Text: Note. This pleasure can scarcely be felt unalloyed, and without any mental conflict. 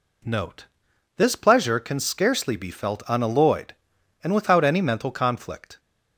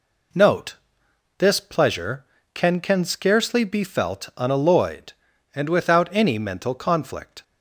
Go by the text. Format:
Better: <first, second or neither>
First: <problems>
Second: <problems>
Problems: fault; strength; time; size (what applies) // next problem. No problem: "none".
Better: first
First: none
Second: says "can" twice; at 2.7 s